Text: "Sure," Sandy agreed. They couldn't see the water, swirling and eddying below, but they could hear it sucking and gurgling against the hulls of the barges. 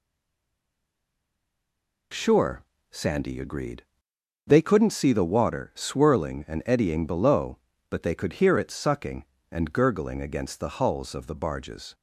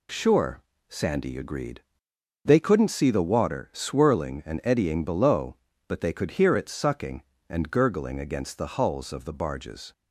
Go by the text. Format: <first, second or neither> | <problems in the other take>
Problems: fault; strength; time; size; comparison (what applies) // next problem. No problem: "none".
second | stays silent before the first word; noticeable; until 2.1 s; 2.1 s long